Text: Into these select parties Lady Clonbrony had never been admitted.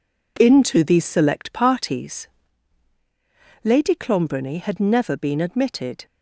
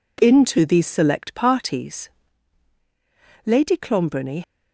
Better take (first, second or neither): first